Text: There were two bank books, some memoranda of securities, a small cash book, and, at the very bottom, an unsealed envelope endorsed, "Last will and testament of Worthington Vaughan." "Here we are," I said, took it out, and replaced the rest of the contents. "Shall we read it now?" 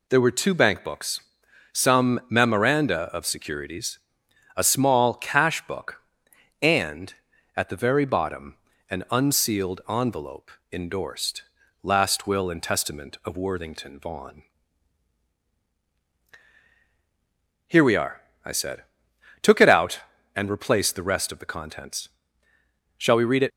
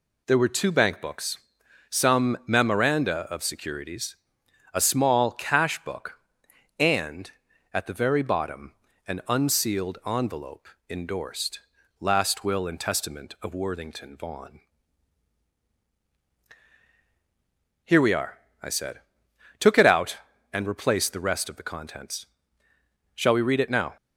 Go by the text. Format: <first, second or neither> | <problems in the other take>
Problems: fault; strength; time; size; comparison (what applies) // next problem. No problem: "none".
second | pauses between "envelope" and "endorsed"; slight; at 10.5 s; 0.20 s long; slight in the second // stops before "now"; at 23.5 s